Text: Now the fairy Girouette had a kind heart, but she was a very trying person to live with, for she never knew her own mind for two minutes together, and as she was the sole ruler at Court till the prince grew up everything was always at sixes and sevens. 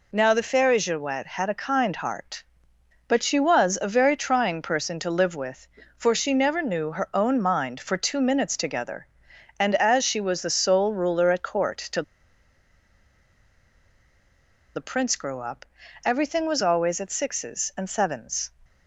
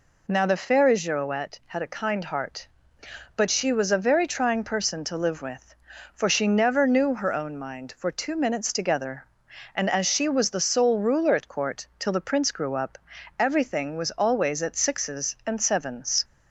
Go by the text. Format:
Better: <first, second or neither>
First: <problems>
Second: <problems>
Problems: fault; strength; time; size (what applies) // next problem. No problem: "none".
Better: second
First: pauses between "till" and "the"; strong; at 12.0 s; 2.7 s long // pauses between "up" and "everything"; at 15.6 s; 0.40 s long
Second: pauses between "up" and "everything"; at 12.9 s; 0.40 s long